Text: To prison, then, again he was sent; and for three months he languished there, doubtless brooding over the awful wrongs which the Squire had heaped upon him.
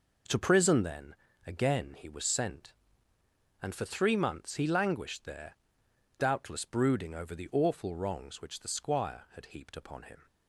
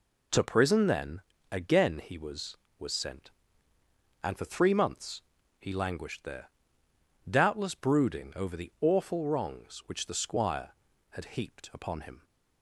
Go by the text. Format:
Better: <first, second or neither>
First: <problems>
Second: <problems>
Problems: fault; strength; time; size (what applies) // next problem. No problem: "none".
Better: first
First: none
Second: says "was" twice; at 2.7 s // pauses between "months" and "he"; slight; at 5.2 s; 0.36 s long